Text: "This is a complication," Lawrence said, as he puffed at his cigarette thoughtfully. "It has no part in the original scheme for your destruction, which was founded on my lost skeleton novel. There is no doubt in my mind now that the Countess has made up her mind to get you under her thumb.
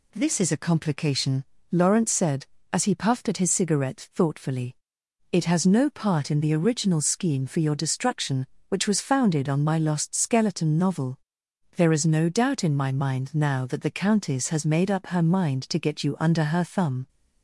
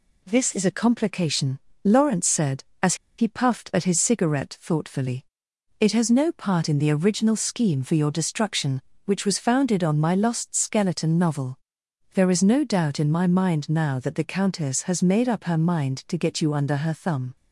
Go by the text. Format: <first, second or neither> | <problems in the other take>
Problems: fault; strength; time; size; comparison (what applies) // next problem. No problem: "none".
first | pauses between "as" and "he"; slight; at 2.9 s; 0.23 s long